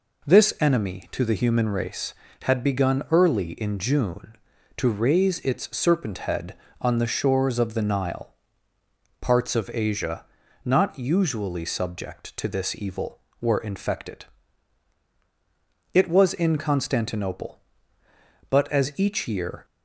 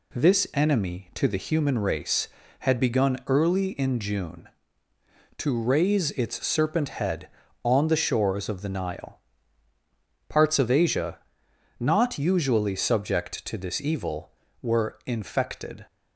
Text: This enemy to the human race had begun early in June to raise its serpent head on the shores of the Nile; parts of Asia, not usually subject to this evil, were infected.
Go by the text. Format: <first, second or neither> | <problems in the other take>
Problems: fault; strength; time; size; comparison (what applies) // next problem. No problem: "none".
second | goes on to say "It was in Constantinople but as each year"; strong; from 15.9 s on; 3.7 s long